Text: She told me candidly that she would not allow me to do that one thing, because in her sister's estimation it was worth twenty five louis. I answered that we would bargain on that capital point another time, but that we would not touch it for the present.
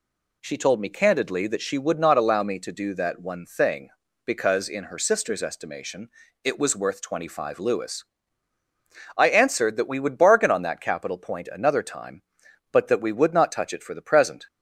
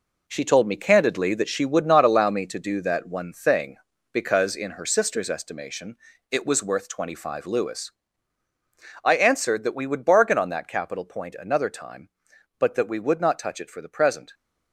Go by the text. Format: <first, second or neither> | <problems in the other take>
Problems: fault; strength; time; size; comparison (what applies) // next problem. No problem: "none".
first | gets quieter; strong; throughout; 8.5 dB // pauses between "estimation" and "it"; slight; at 5.9 s; 0.34 s long; slight in the first